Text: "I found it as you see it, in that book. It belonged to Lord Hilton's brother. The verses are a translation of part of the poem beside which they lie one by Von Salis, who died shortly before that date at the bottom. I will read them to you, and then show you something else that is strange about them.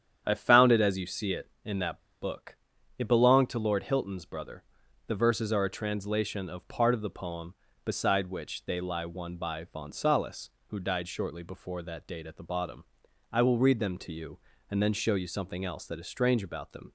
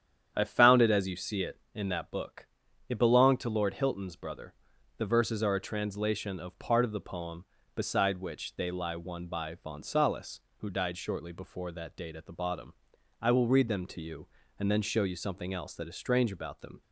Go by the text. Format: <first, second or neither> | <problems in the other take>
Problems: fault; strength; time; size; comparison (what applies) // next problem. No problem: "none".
second | starts louder than the rest; strong; until 1.2 s; 9 dB; strong in the second // pauses between "that" and "book"; slight; at 2.0 s; 0.19 s long